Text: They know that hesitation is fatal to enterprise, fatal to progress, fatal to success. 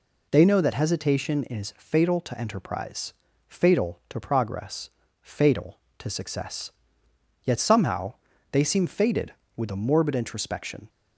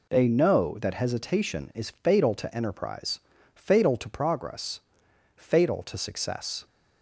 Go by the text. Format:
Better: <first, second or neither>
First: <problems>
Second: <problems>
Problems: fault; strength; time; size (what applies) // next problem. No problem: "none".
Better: second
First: goes on to say "Yet somehow they seem fated with a morbid introspection"; strong; from 7.4 s on; 3.4 s long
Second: none